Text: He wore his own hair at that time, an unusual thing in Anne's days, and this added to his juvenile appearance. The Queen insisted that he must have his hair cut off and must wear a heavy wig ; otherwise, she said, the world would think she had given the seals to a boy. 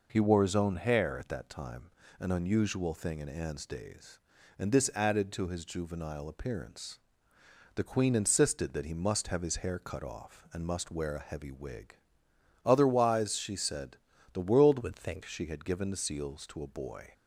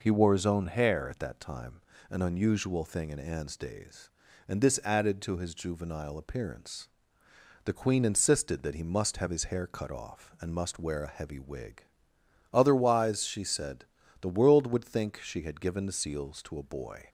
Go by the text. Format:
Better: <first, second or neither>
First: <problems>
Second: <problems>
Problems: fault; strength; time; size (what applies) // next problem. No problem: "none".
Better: second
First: changes voice from "would" to "think"; from 14.8 to 15.2 s; 0.4 s long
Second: none